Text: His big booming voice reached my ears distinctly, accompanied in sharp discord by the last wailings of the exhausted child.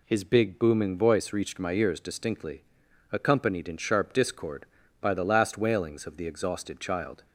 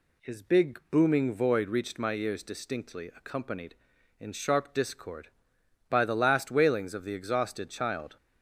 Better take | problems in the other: first | says "void" for "voice"; at 1.3 s

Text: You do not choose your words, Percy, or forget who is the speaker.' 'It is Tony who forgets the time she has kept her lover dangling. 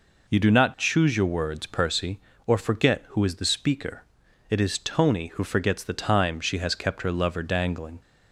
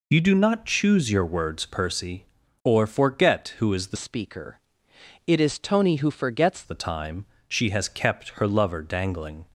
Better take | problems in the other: first | changes voice from "speaker" to "forgets"; from 3.9 to 6.6 s; 2.7 s long // pauses between "time" and "she"; slight; at 7.2 s; 0.22 s long

